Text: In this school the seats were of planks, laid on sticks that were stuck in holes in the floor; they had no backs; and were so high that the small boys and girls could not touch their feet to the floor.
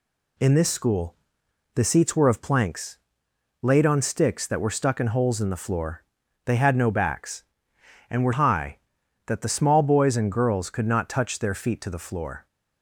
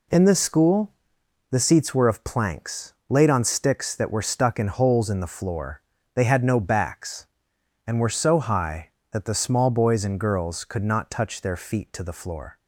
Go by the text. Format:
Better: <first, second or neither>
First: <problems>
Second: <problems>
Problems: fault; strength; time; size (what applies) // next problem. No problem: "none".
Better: second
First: pauses between "school" and "the"; noticeable; at 1.1 s; 0.58 s long // skips "so"; at 8.3 s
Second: pauses between "school" and "the"; noticeable; at 0.9 s; 0.60 s long